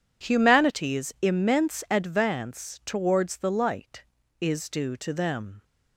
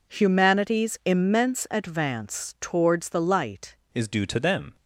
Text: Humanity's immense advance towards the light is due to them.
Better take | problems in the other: first | changes voice at "is"; from 3.9 s on; 0.8 s long

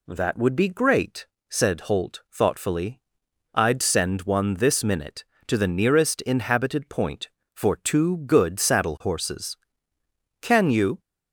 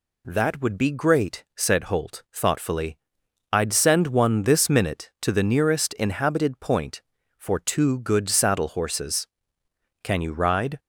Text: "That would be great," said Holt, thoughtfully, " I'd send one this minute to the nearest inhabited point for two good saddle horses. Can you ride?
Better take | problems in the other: second | stops before "ride"; at 10.9 s

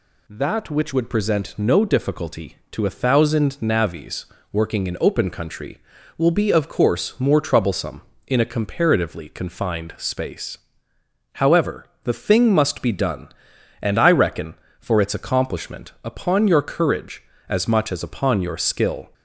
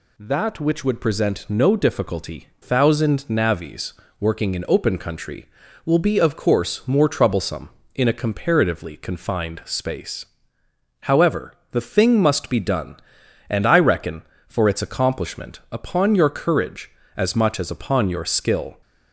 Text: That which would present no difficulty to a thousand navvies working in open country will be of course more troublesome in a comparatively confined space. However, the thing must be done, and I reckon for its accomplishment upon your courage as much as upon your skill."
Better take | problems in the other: first | skips "to a"; at 2.5 s // pauses between "navvies" and "working"; slight; at 3.9 s; 0.28 s long; slight in the first

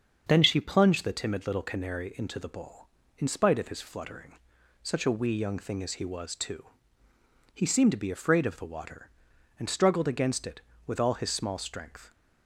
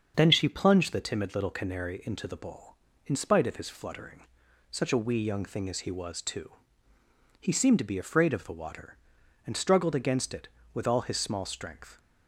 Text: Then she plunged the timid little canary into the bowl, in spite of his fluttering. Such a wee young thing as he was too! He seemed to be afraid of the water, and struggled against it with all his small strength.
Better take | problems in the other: neither | starts louder than the rest; the same in both

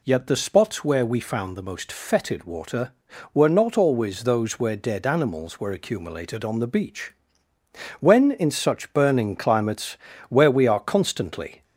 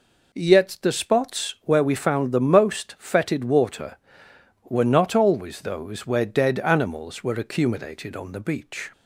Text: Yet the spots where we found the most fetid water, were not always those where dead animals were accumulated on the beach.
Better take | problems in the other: second | goes on to say "When in such burning climates where we are constantly"; strong; from 7.9 s on; 3.6 s long

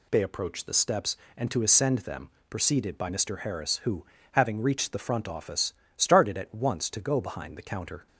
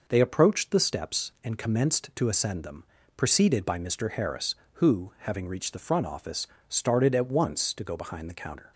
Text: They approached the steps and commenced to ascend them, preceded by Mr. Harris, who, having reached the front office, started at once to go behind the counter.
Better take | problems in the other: second | skips "commenced"; at 1.5 s

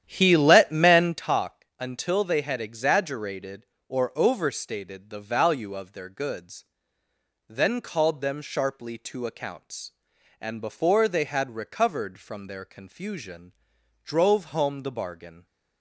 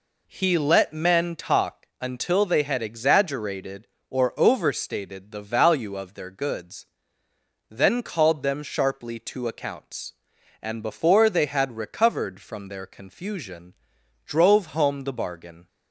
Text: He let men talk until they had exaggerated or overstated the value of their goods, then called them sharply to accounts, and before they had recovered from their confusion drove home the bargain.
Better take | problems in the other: second | starts louder than the rest; strong; until 1.3 s; 10.5 dB // pauses between "confusion" and "drove"; noticeable; at 13.5 s; 0.52 s long; noticeable in the second

